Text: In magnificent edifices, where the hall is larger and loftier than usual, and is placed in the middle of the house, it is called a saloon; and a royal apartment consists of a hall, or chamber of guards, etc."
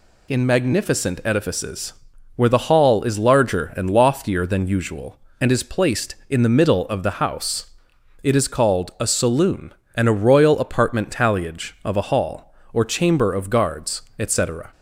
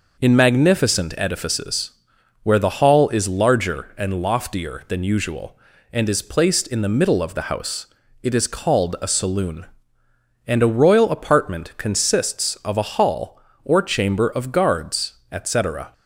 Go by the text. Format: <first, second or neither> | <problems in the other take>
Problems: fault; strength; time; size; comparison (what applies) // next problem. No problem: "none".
second | says "talliage" for "consists"; at 11.0 s